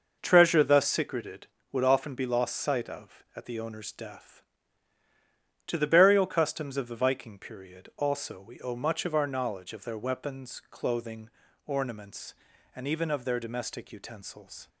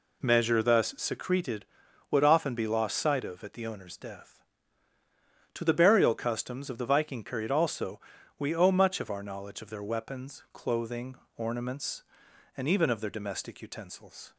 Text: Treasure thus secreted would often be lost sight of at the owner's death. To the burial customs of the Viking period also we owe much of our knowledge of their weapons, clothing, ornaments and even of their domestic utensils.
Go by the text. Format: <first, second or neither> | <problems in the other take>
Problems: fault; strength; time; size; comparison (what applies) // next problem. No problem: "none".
first | says "Measure" for "Treasure"; at 0.2 s // pauses between "also" and "we"; at 7.9 s; 0.40 s long